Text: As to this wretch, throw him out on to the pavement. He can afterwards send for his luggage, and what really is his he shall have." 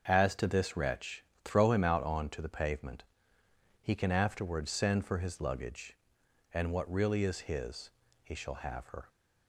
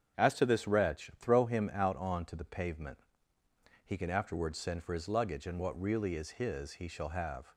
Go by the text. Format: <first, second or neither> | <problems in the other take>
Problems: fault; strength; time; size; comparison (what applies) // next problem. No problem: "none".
second | starts louder than the rest; until 1.0 s; 6.5 dB; strong in the second // pauses between "his" and "he"; slight; at 7.9 s; 0.34 s long // goes on to say "Her"; slight; from 8.8 s on; 0.22 s long